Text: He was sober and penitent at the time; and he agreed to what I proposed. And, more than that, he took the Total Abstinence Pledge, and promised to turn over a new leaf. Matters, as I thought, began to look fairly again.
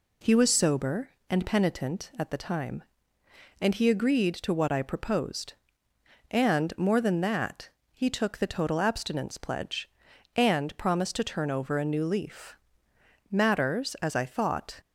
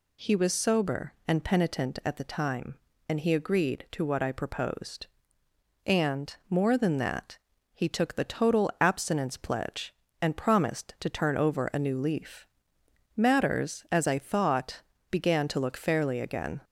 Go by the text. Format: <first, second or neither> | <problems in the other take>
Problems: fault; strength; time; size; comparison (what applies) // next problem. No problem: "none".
second | stops before "began to look fairly again"; at 14.7 s